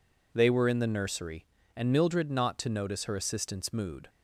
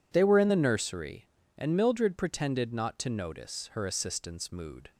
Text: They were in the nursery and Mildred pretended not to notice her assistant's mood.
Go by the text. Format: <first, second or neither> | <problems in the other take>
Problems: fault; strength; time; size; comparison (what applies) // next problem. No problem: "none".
second | skips "pretended"; at 2.3 s